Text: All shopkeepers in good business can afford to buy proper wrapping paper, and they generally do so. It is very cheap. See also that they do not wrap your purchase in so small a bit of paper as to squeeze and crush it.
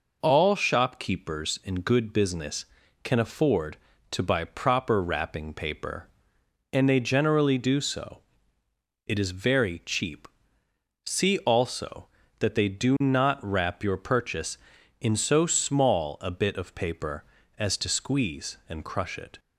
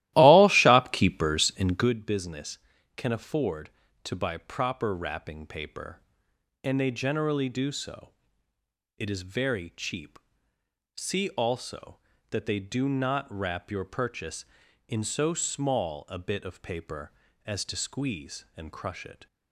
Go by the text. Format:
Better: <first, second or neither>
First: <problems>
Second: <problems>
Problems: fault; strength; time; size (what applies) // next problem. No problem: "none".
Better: first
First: none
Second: starts louder than the rest; strong; until 2.0 s; 15.5 dB